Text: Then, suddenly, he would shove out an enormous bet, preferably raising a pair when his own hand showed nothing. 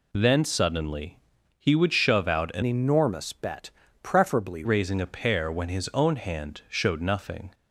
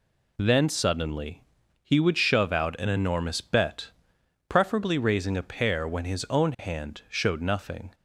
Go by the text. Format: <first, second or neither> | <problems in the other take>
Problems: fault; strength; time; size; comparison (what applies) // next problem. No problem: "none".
second | changes voice from "enormous" to "preferably"; from 2.6 to 4.6 s; 2.0 s long